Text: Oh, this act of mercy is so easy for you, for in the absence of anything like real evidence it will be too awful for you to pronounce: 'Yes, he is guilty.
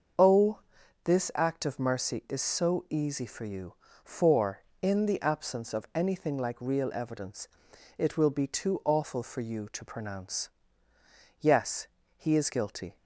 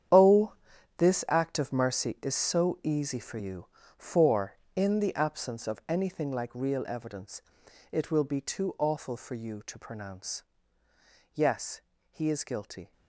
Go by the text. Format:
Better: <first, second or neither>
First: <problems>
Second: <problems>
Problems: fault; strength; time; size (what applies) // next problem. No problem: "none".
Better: first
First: starts louder than the rest; until 1.6 s; 6 dB // pauses between "evidence" and "it"; noticeable; at 7.4 s; 0.50 s long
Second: gets quieter; strong; throughout; 14 dB // starts louder than the rest; strong; until 1.6 s; 9 dB // pauses between "evidence" and "it"; noticeable; at 7.4 s; 0.50 s long